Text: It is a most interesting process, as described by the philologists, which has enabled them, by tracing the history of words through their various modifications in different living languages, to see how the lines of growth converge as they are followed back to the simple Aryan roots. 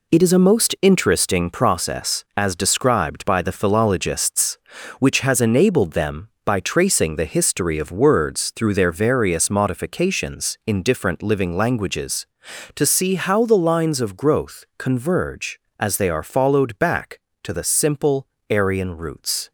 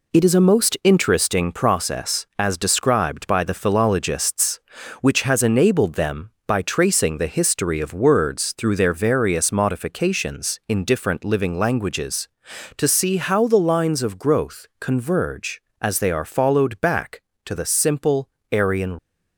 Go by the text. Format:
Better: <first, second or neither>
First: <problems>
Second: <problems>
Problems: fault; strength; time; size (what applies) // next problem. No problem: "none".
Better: first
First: pauses between "simple" and "Aryan"; slight; at 18.2 s; 0.24 s long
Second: pauses between "simple" and "Aryan"; slight; at 18.2 s; 0.24 s long // stops before "roots"; at 18.9 s